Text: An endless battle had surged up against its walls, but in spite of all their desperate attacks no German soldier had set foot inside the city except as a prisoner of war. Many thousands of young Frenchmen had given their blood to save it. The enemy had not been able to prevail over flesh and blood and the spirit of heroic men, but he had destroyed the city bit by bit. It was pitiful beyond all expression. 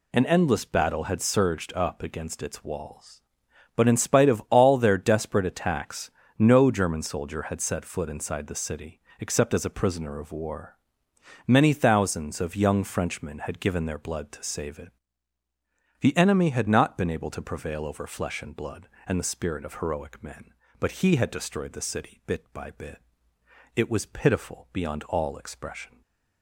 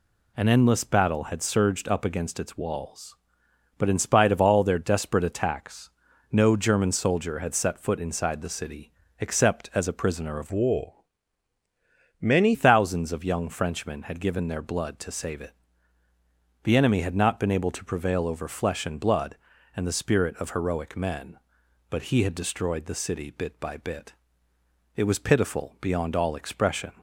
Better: first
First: pauses between "attacks" and "no"; slight; at 6.0 s; 0.30 s long // pauses between "city" and "except"; slight; at 8.9 s; 0.20 s long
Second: pauses between "attacks" and "no"; at 5.8 s; 0.44 s long // pauses between "city" and "except"; slight; at 8.9 s; 0.28 s long // changes voice from "war" to "Many"; from 10.5 to 12.5 s; 2.0 s long

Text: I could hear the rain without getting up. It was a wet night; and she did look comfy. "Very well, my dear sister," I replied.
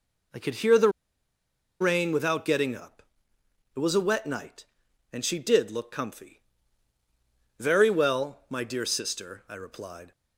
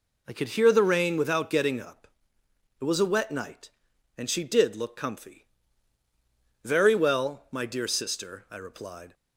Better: second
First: pauses between "the" and "rain"; noticeable; at 0.8 s; 0.91 s long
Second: none

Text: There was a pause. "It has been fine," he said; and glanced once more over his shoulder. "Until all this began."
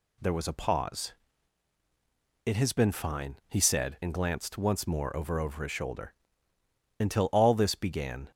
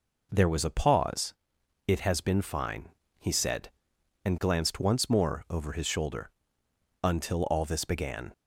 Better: second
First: says "over" twice; at 5.3 s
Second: none

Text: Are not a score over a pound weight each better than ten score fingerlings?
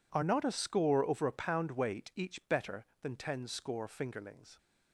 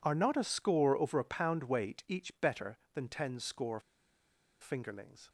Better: first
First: none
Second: pauses between "score" and "fingerlings"; noticeable; at 3.7 s; 0.81 s long

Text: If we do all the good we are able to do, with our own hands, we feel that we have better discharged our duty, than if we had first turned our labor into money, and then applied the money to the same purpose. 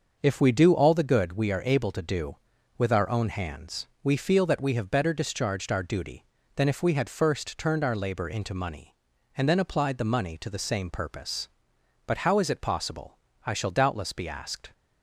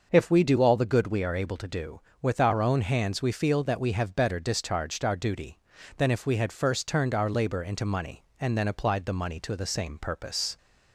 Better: second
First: starts louder than the rest; until 1.2 s; 6.5 dB // goes on to say "But how is it possible I shall doubtless be asked"; strong; from 12.0 s on; 2.6 s long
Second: starts louder than the rest; until 1.1 s; 6 dB

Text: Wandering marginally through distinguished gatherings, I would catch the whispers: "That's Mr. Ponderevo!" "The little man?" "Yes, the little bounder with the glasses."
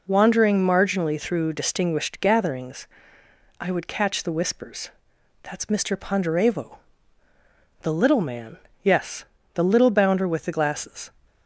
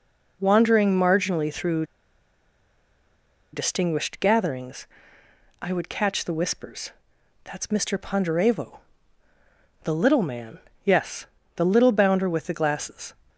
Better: first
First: none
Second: pauses between "through" and "distinguished"; strong; at 1.8 s; 1.6 s long

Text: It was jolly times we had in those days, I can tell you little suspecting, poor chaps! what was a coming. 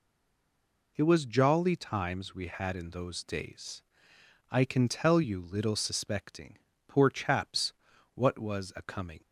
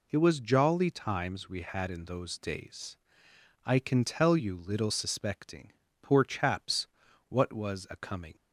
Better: second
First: stays silent before the first word; slight; until 0.9 s; 0.9 s long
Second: none

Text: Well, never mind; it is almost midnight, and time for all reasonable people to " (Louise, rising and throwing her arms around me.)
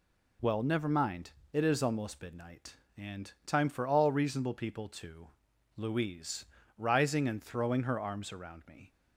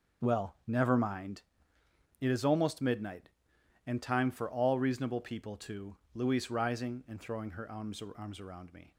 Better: first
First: none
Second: starts louder than the rest; until 1.3 s; 6.5 dB // says "arms" twice; at 8.1 s

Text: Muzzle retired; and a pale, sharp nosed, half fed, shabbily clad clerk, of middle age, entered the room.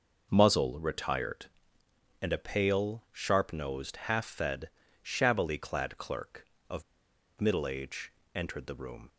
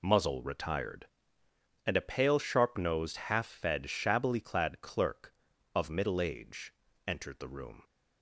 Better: second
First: pauses between "of" and "middle"; noticeable; at 6.8 s; 0.57 s long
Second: none

